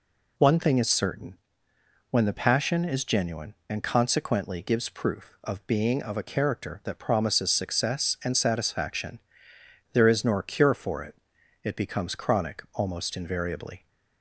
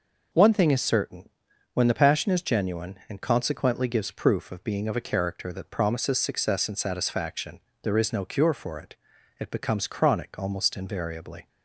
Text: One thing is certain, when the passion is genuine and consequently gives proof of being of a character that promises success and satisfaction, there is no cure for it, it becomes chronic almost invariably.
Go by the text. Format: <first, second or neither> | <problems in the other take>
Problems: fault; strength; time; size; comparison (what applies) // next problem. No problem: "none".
second | says "nor" for "no"; at 10.2 s